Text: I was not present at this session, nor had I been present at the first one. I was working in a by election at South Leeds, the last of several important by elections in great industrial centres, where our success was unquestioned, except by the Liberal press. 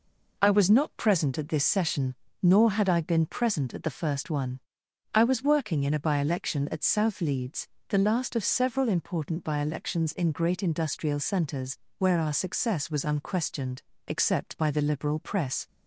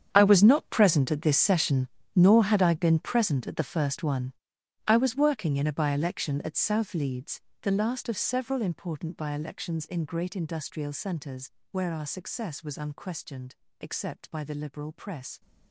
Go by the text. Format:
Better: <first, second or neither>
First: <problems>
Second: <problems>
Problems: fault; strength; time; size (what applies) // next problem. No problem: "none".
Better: first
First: none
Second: gets quieter; strong; throughout; 17 dB